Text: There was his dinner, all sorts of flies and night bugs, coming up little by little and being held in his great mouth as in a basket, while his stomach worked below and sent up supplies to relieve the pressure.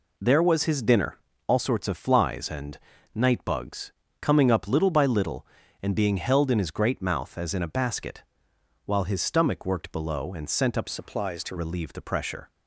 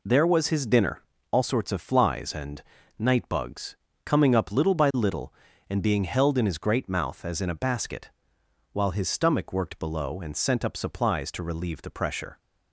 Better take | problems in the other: second | pauses between "and" and "night"; slight; at 2.7 s; 0.34 s long; slight in the second // changes voice from "supplies" to "to"; from 10.8 to 11.5 s; 0.7 s long

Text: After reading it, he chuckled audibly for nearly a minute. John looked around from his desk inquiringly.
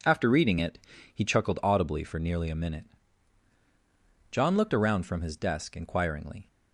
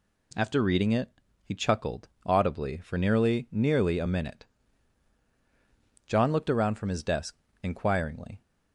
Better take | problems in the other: first | pauses between "chuckled" and "audibly"; slight; at 2.0 s; 0.16 s long // says "nearly" twice; at 3.5 s // pauses between "desk" and "inquiringly"; slight; at 7.3 s; 0.28 s long

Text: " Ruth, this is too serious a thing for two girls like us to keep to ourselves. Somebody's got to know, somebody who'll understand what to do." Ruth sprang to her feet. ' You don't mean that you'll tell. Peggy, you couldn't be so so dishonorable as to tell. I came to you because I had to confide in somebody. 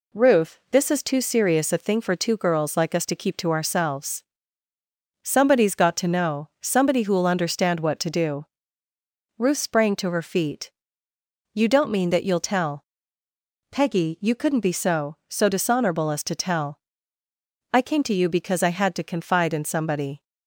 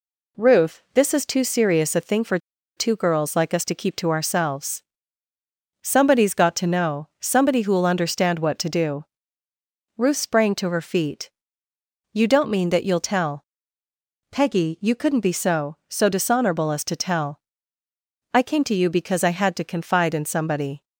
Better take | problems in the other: first | pauses between "for" and "two"; at 2.3 s; 0.39 s long

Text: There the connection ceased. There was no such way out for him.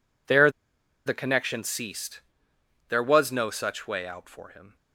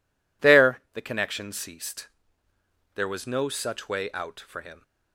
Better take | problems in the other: second | pauses between "There" and "the"; noticeable; at 0.4 s; 0.56 s long

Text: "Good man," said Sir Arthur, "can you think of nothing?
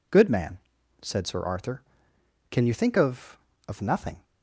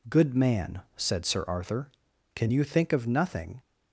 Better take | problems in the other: second | says "of" twice; at 3.6 s

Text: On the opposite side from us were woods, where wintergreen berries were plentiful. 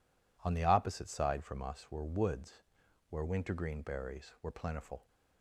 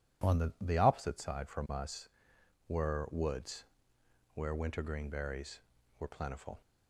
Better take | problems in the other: first | says "the" twice; at 0.6 s

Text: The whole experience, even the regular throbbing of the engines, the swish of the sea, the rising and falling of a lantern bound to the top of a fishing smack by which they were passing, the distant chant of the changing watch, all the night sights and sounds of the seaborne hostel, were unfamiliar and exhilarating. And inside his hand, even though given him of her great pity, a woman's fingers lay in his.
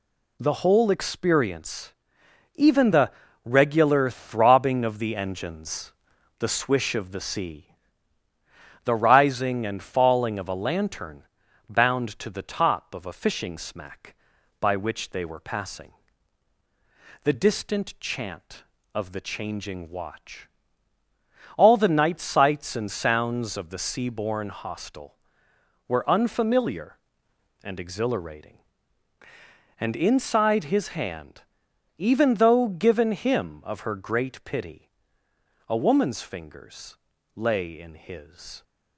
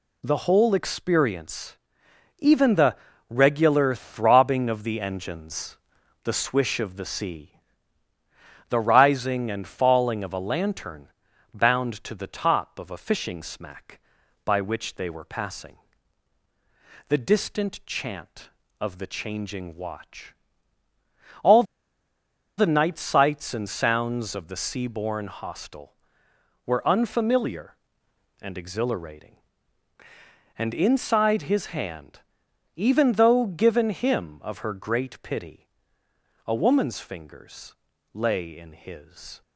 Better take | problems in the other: first | pauses between "the" and "regular"; slight; at 2.9 s; 0.32 s long; slight in the first // pauses between "lantern" and "bound"; noticeable; at 11.0 s; 0.48 s long; noticeable in the first // pauses between "all" and "the"; noticeable; at 21.6 s; 0.94 s long // pauses between "fingers" and "lay"; at 37.7 s; 0.40 s long; also in the first

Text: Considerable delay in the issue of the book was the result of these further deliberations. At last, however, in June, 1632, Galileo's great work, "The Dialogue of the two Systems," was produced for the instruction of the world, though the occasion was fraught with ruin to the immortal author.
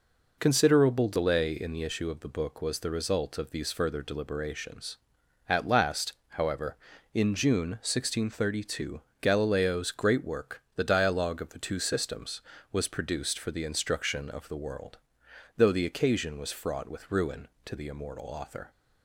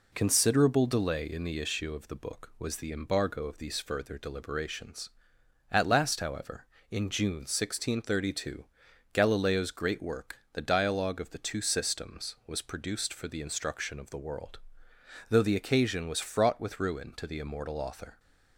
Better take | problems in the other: first | says "embargo" for "result"; at 2.9 s

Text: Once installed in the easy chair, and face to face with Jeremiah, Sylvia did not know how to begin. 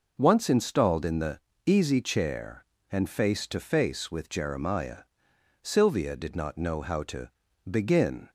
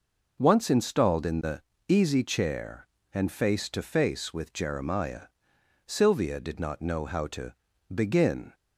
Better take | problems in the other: neither | pauses between "the" and "easy"; slight; the same in both // pauses between "to" and "begin"; the same in both

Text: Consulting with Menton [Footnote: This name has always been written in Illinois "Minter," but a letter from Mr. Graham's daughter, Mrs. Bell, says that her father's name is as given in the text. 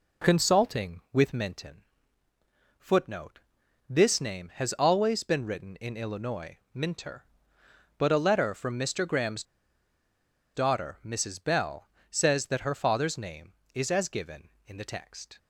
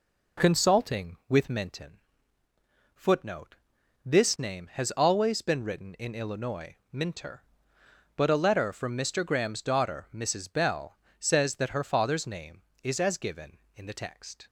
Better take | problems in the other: second | pauses between "Menton" and "Footnote"; noticeable; at 1.8 s; 0.98 s long; noticeable in the second // pauses between "Graham's" and "daughter"; at 9.4 s; 1.1 s long

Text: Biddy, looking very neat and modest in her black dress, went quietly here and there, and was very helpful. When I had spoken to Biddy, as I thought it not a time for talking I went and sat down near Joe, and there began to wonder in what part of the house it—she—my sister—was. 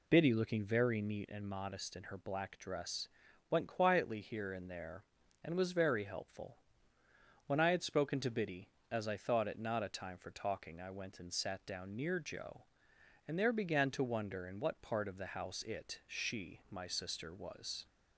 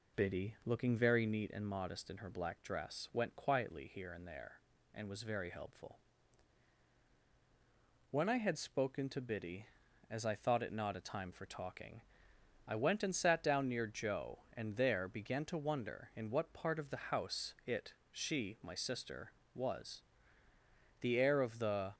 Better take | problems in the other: first | pauses between "talking" and "I"; noticeable; at 12.0 s; 0.64 s long // goes on to say "The air of the"; noticeable; from 21.0 s on; 0.94 s long

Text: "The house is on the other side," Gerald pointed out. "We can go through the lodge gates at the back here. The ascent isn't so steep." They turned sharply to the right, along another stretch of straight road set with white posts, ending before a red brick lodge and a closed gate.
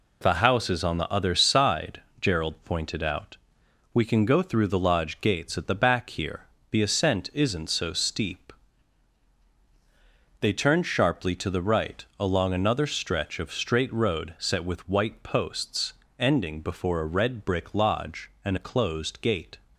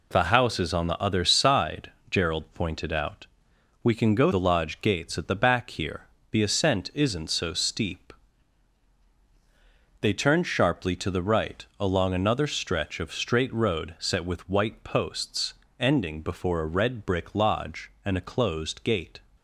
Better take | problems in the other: first | skips "through"; at 4.3 s

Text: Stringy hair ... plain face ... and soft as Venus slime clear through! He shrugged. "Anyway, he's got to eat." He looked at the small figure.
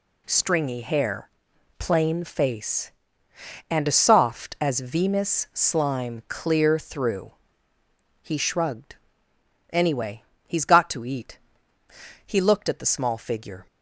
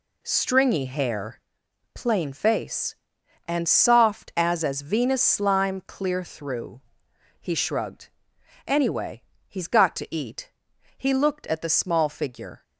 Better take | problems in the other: first | says "as" twice; at 4.6 s

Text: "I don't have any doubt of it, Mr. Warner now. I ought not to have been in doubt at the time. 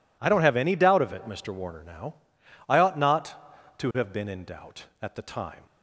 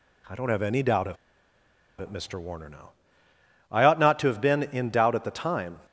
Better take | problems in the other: first | pauses between "of" and "it"; noticeable; at 1.1 s; 0.84 s long

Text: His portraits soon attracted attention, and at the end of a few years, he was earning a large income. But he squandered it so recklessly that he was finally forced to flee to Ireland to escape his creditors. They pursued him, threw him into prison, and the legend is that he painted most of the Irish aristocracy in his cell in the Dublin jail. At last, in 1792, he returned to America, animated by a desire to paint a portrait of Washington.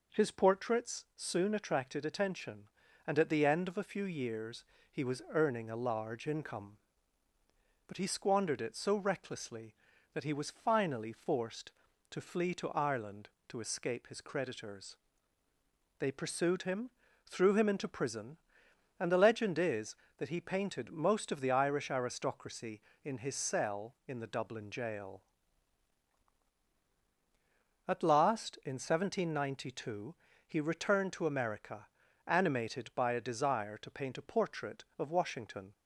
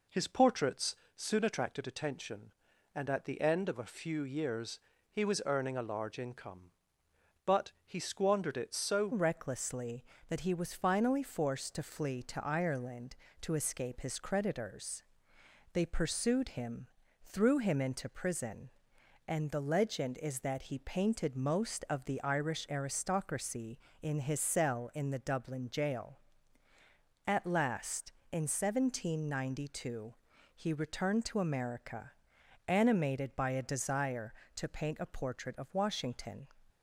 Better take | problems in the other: first | pauses between "portraits" and "soon"; slight; at 0.9 s; 0.20 s long // changes voice at "recklessly"; from 9.1 s on; 27.3 s long

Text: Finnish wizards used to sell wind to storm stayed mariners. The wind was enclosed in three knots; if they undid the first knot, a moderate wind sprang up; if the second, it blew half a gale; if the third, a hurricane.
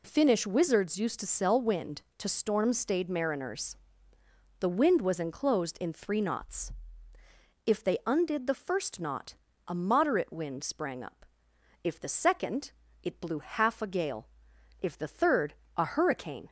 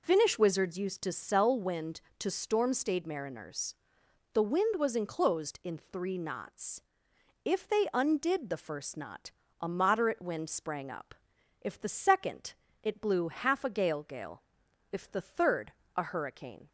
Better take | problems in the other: first | says "gale" twice; at 14.0 s

